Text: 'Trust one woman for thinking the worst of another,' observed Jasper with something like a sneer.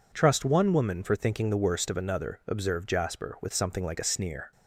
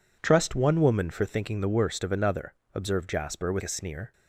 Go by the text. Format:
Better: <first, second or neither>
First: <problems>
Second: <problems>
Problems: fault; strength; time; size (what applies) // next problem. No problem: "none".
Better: first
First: none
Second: skips "something like"; at 3.6 s